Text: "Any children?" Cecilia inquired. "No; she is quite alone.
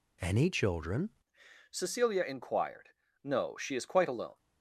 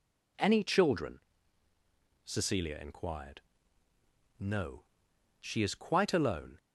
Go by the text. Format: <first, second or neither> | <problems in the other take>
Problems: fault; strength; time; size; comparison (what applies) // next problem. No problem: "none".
second | changes voice at "Cecilia"; from 1.6 s on; 2.7 s long